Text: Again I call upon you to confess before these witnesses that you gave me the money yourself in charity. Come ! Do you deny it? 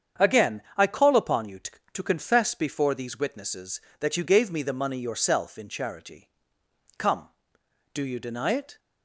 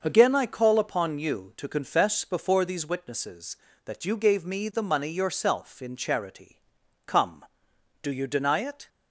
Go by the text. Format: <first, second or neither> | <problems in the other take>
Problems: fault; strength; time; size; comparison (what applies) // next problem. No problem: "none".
second | starts louder than the rest; strong; until 1.3 s; 7.5 dB; also in the second // says "to" twice; at 1.9 s